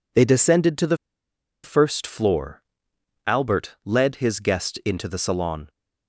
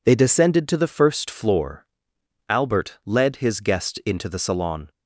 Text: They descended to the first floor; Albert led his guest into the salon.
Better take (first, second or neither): second